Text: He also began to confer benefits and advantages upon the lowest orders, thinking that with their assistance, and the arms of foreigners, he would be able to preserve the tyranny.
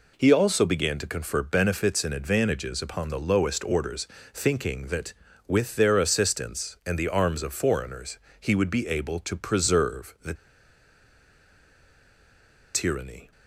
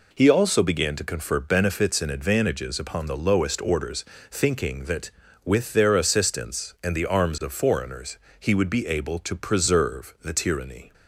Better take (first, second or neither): second